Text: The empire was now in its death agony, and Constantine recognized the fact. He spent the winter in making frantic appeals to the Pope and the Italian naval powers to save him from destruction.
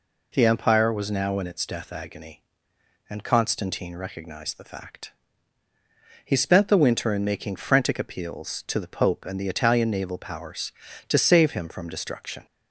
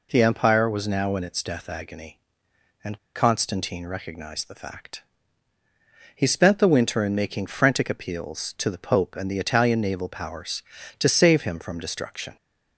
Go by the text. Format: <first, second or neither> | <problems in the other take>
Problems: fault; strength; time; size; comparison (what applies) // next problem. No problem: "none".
first | pauses between "and" and "Constantine"; slight; at 2.9 s; 0.17 s long